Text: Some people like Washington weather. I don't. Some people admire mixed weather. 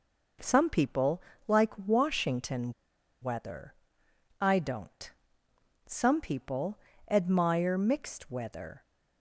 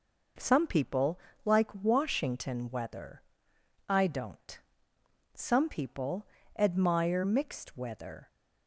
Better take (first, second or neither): second